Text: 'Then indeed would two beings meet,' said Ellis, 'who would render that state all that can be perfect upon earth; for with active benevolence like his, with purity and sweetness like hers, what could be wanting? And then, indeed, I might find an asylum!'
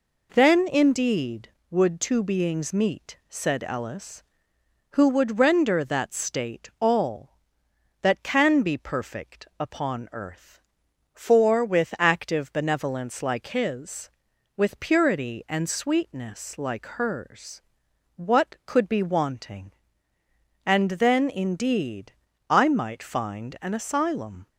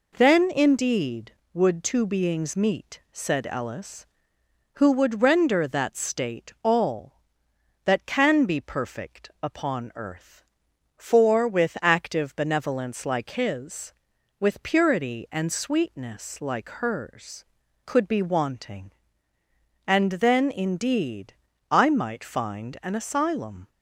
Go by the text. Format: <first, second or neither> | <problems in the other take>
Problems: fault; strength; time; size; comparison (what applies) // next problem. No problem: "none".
first | skips "what"; at 17.6 s